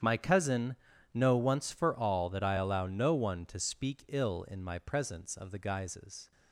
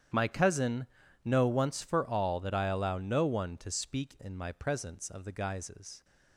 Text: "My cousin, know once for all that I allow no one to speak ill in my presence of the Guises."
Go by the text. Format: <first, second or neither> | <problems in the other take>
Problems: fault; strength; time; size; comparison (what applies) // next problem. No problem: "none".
first | starts louder than the rest; strong; until 1.5 s; 9.5 dB; strong in the first // skips "ill"; at 4.1 s